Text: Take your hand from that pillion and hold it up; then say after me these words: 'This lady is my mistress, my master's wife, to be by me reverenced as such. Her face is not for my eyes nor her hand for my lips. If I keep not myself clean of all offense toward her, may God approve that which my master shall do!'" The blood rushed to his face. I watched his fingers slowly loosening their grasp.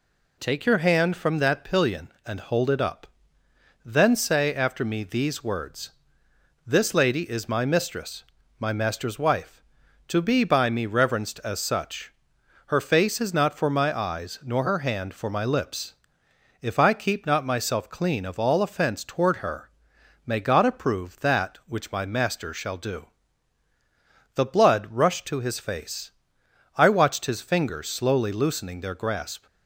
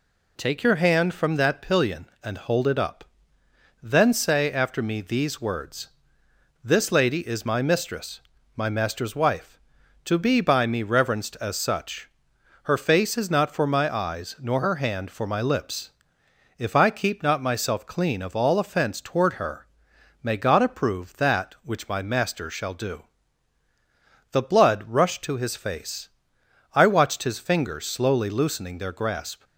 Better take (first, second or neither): neither